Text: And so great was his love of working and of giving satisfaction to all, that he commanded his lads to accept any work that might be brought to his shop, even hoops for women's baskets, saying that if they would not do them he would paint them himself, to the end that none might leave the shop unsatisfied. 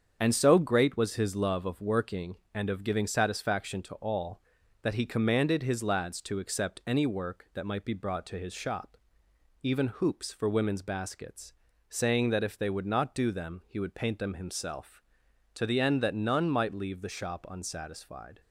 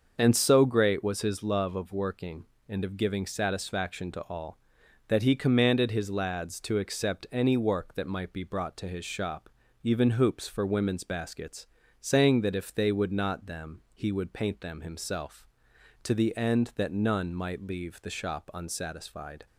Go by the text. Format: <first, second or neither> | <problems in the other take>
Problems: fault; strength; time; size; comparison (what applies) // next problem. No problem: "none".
first | starts louder than the rest; until 1.1 s; 6.5 dB; strong in the first // skips "do"; at 13.4 s